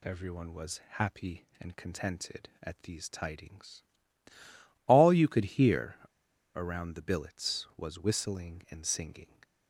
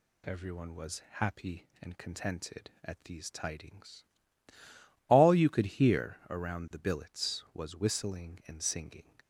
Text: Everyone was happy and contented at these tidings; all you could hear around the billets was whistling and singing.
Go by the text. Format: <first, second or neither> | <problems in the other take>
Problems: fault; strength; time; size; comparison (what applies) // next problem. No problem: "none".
second | pauses between "was" and "happy"; slight; at 0.8 s; 0.16 s long; slight in the second // pauses between "hear" and "around"; noticeable; at 5.9 s; 0.61 s long